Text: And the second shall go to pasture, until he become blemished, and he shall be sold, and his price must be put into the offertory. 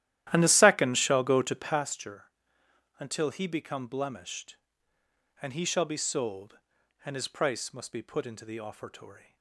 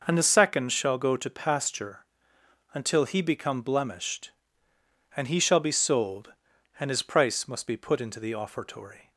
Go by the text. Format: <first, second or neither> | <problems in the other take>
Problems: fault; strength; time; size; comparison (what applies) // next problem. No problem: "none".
second | starts louder than the rest; strong; until 1.8 s; 13 dB